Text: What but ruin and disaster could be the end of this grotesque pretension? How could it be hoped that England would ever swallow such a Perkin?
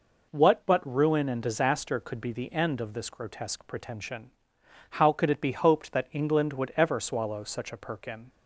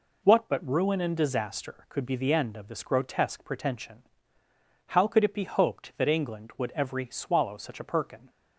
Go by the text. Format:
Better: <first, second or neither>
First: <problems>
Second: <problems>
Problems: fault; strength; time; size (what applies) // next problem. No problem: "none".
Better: first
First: none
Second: says "every" for "ever"; at 6.7 s